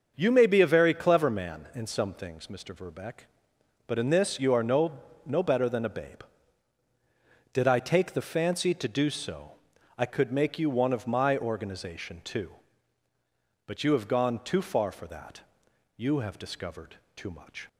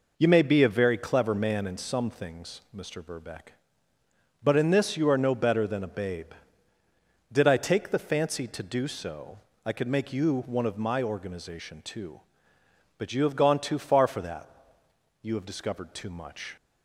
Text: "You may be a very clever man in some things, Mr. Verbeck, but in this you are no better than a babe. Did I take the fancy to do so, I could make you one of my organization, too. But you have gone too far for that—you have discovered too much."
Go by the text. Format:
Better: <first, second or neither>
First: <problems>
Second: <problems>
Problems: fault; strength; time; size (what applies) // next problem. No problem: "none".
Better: second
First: starts louder than the rest; until 1.1 s; 6.5 dB // says "no" twice; at 5.2 s // pauses between "discovered" and "too"; slight; at 16.9 s; 0.20 s long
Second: none